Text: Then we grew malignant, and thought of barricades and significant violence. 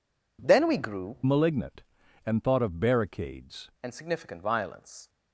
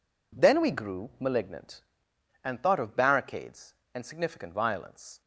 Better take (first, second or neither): second